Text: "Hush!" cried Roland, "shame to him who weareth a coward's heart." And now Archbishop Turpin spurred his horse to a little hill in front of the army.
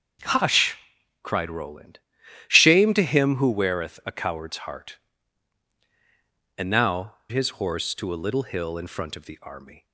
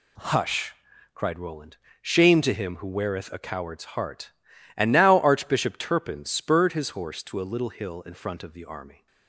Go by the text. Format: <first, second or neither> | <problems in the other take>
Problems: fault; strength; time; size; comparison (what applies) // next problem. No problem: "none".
second | starts louder than the rest; until 1.6 s; 6.5 dB // skips "Archbishop Turpin spurred"; at 7.2 s